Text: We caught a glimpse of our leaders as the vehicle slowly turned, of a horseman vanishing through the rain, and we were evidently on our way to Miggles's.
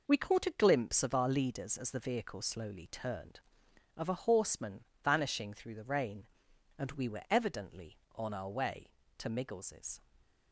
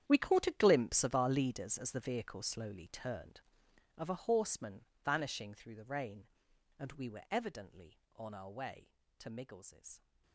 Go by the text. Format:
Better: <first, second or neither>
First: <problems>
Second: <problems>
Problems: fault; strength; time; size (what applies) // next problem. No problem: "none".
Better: first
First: pauses between "horseman" and "vanishing"; slight; at 4.8 s; 0.20 s long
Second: gets quieter; strong; throughout; 16.5 dB // pauses between "horseman" and "vanishing"; slight; at 4.8 s; 0.20 s long